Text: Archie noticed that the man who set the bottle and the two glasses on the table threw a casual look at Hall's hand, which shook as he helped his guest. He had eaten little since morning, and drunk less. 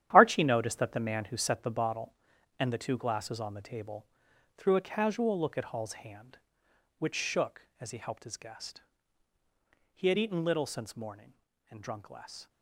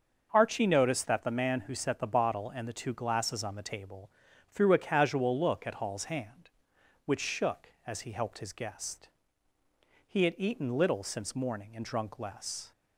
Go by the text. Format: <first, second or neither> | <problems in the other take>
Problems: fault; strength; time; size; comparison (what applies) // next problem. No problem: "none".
second | gets quieter; strong; throughout; 11 dB // starts louder than the rest; strong; until 1.1 s; 11 dB; also in the second // pauses between "table" and "threw"; noticeable; at 4.0 s; 0.52 s long; also in the second